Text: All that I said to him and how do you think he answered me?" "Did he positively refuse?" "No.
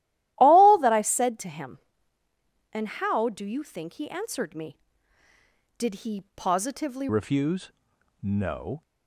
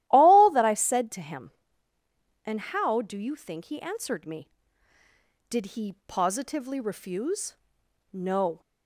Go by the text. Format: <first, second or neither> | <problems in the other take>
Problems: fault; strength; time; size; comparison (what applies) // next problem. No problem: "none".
second | starts louder than the rest; strong; until 1.3 s; 14.5 dB; strong in the second // changes voice at "refuse"; from 7.0 s on; 1.8 s long